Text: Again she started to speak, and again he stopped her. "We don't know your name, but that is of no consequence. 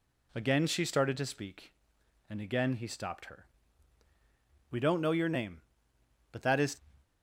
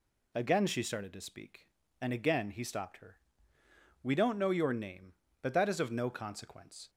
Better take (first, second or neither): second